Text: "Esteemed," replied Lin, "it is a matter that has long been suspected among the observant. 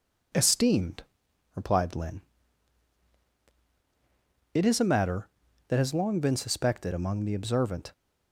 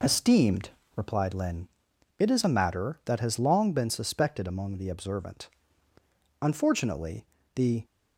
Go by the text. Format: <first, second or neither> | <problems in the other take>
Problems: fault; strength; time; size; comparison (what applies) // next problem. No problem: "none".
first | goes on to say "Unfortunately the"; from 6.4 s on; 1.4 s long